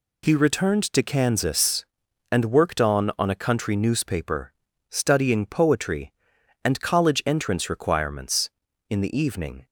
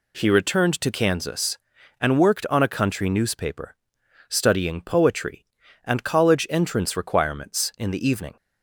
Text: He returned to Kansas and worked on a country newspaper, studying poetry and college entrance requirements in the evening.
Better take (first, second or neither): second